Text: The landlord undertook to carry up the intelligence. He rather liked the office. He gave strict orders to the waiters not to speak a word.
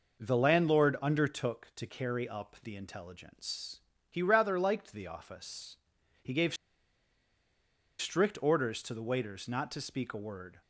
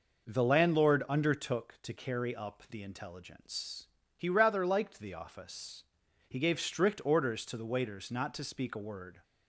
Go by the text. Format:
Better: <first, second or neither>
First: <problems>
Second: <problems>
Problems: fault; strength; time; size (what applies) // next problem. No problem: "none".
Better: second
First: pauses between "gave" and "strict"; strong; at 6.5 s; 1.4 s long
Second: none